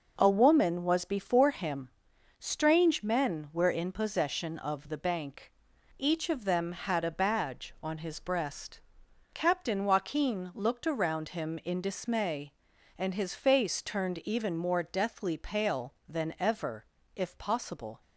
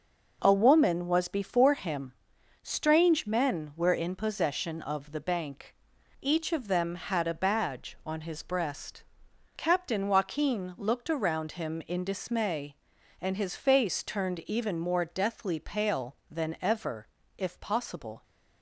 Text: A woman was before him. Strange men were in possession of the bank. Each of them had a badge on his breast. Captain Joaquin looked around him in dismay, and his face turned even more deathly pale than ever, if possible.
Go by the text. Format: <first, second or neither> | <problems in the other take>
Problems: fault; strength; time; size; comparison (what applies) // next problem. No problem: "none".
neither | starts louder than the rest; the same in both